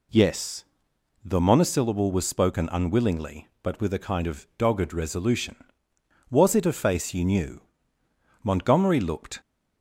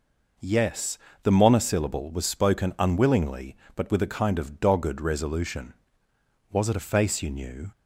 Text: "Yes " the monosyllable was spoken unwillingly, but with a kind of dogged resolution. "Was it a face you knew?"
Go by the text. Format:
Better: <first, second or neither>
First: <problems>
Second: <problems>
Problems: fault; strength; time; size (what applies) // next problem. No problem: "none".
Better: second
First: goes on to say "Montgomery looked"; noticeable; from 8.4 s on; 0.98 s long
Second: none